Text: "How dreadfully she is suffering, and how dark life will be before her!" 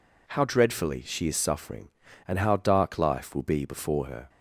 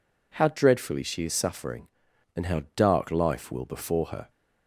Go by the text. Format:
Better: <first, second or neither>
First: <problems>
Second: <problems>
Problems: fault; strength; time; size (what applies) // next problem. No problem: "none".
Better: first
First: none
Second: skips "be"; at 3.6 s